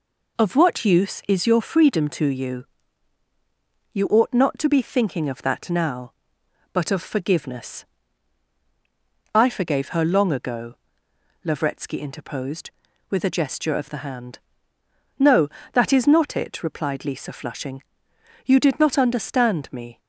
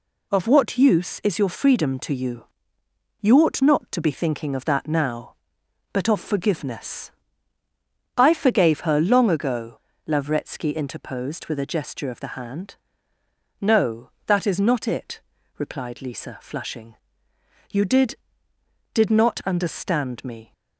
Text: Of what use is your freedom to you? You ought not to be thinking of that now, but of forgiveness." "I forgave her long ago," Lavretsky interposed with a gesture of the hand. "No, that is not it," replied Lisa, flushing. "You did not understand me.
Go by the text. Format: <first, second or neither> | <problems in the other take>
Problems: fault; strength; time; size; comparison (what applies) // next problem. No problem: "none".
first | says "did" twice; at 18.9 s